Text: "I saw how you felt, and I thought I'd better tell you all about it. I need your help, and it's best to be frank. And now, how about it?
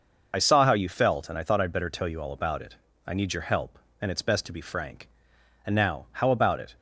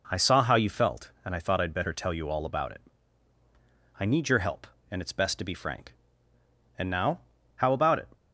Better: second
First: loses the start of "I"; at 0.3 s; 45 ms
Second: none

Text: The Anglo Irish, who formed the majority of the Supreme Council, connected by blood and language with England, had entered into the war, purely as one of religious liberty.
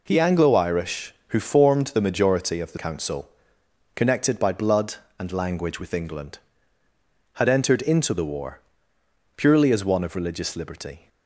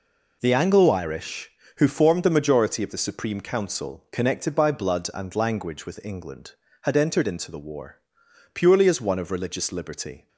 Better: second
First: skips "Supreme"; at 2.7 s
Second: none

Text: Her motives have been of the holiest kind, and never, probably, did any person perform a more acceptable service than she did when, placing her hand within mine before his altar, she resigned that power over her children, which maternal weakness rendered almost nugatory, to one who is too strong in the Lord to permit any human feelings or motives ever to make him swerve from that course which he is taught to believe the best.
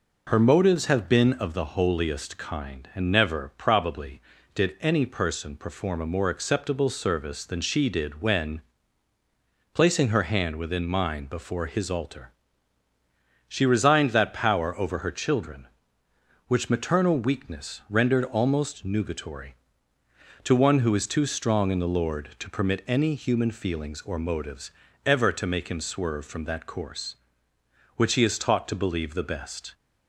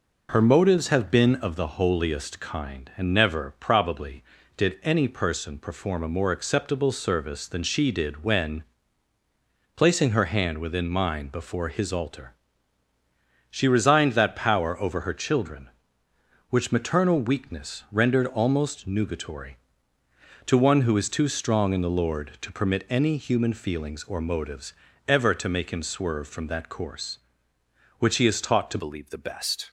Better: first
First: pauses between "motives" and "ever"; slight; at 24.7 s; 0.34 s long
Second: pauses between "motives" and "ever"; slight; at 24.7 s; 0.34 s long // changes voice at "believe"; from 28.7 s on; 0.9 s long

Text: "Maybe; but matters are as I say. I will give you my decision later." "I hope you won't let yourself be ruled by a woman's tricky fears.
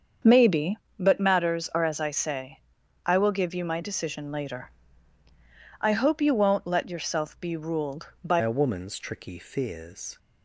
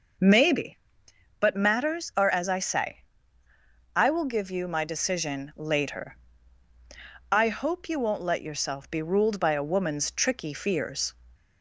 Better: second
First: starts louder than the rest; until 1.4 s; 7 dB // changes voice at "a"; from 8.4 s on; 1.7 s long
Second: none

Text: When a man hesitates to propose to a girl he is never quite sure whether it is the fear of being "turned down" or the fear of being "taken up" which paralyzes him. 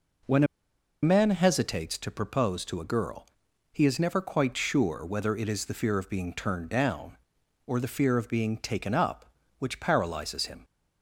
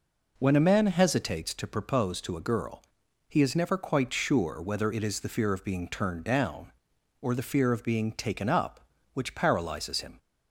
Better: second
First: pauses between "a" and "man"; noticeable; at 0.4 s; 0.58 s long // pauses between "girl" and "he"; at 3.2 s; 0.44 s long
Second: pauses between "girl" and "he"; at 2.8 s; 0.44 s long

